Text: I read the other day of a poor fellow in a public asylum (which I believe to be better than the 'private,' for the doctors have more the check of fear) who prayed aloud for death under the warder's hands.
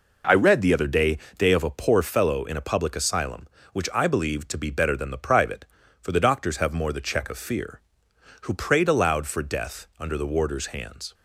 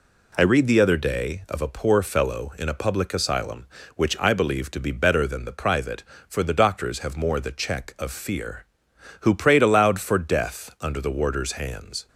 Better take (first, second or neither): second